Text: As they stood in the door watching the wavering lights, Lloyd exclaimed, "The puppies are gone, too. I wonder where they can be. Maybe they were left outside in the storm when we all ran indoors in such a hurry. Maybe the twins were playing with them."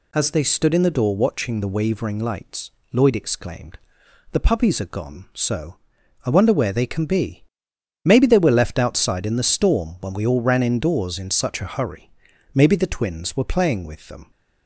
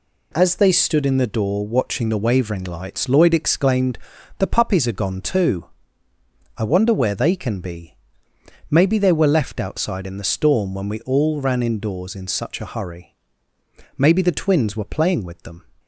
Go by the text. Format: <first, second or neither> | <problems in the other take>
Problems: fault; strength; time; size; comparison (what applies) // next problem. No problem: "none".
second | says "so" for "too"; at 5.3 s